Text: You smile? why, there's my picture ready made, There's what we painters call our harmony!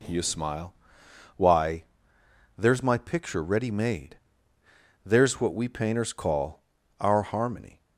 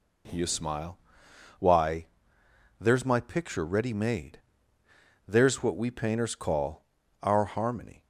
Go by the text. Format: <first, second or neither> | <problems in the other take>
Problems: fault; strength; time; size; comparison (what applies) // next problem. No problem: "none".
neither | pauses between "call" and "our"; the same in both